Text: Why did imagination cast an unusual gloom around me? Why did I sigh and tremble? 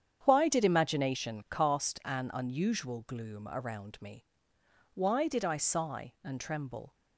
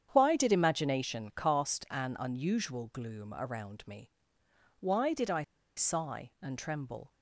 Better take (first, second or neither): first